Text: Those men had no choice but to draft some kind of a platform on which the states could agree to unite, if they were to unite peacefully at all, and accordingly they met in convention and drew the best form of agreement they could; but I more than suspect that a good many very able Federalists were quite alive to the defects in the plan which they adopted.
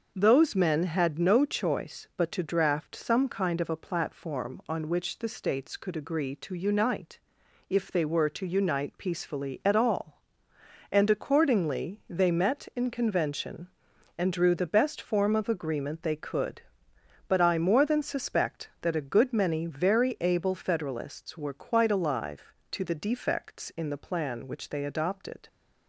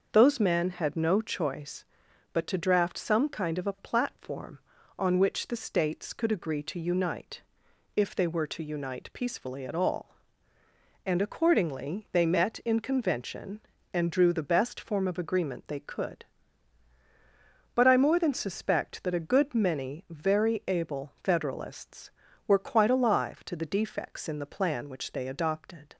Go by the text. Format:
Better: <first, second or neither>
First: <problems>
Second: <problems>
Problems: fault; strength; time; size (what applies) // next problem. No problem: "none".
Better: neither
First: starts louder than the rest; noticeable; until 1.1 s; 6 dB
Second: starts louder than the rest; until 1.1 s; 6 dB